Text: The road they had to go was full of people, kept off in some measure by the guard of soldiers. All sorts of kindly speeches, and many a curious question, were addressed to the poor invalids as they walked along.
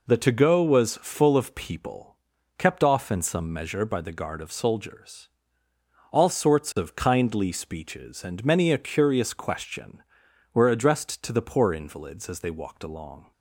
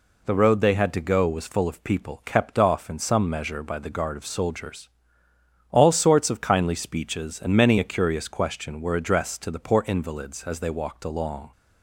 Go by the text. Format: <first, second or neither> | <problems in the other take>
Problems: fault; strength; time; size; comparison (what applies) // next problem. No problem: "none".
second | skips "road they had"; at 0.1 s